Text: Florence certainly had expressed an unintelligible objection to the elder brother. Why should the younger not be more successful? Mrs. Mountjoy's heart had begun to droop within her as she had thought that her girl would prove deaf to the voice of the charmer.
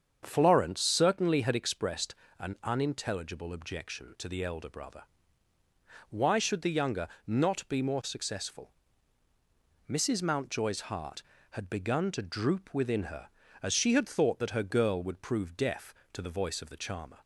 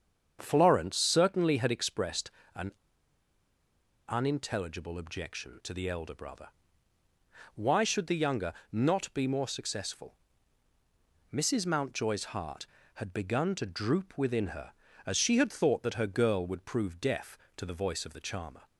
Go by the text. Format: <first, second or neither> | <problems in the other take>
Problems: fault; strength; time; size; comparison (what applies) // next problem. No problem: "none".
first | starts louder than the rest; strong; until 1.4 s; 7.5 dB; strong in the first // pauses between "expressed" and "an"; slight; at 2.2 s; 0.24 s long; slight in the first // pauses between "an" and "unintelligible"; strong; at 2.7 s; 1.3 s long // pauses between "younger" and "not"; slight; at 8.5 s; 0.18 s long; slight in the first